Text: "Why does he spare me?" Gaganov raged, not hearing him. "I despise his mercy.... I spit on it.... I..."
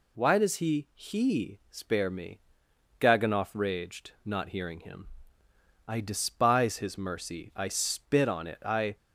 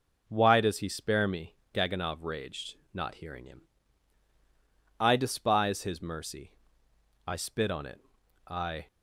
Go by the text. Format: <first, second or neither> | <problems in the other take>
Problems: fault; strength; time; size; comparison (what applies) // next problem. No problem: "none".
second | says "he" twice; at 0.9 s